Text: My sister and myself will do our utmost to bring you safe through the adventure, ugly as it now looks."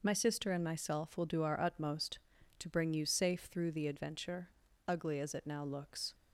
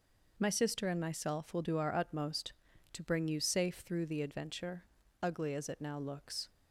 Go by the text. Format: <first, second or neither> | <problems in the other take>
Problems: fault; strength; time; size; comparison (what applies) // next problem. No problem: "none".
neither | none